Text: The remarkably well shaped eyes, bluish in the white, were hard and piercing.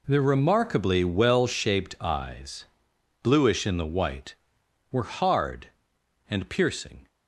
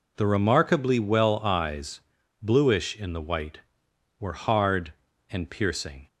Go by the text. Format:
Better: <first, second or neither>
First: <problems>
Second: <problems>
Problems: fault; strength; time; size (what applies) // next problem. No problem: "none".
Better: first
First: none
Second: skips "shaped"; at 1.3 s